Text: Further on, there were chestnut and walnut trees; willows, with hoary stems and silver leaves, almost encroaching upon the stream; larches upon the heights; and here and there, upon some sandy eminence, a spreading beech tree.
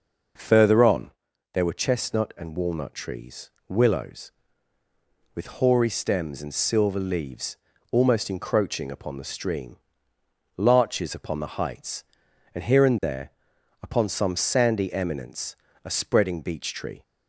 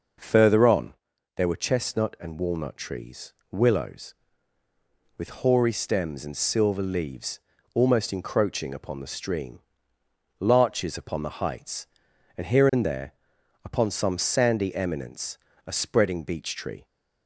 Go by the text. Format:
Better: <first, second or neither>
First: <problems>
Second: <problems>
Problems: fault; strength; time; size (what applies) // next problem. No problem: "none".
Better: neither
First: none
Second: none